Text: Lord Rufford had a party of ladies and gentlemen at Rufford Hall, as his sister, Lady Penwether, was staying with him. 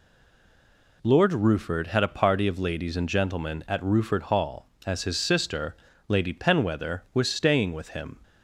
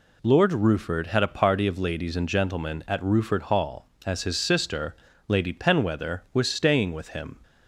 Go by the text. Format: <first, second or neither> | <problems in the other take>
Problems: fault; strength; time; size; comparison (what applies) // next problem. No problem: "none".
second | stays silent before the first word; until 1.0 s; 1.0 s long